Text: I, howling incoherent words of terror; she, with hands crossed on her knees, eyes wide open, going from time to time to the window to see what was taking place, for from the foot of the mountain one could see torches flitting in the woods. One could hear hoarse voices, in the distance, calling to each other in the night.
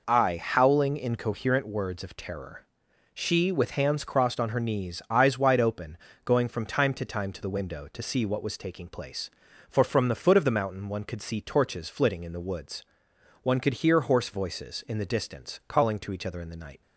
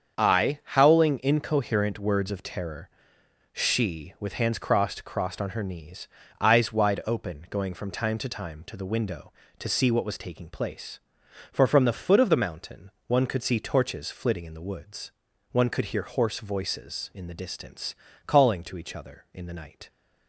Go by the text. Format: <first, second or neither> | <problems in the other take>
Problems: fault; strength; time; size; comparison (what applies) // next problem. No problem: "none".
first | starts louder than the rest; strong; until 1.2 s; 7 dB // says "crossed" twice; at 5.0 s // pauses between "mountain" and "one"; slight; at 12.9 s; 0.16 s long